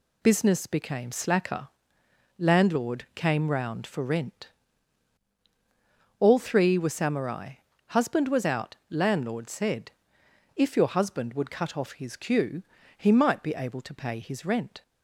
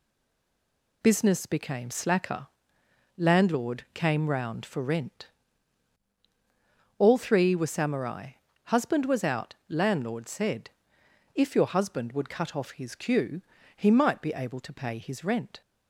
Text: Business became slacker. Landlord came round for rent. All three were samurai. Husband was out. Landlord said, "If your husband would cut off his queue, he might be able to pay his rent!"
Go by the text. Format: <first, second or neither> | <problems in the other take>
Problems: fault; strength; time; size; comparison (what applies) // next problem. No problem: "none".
first | stays silent before the first word; until 1.0 s; 1.0 s long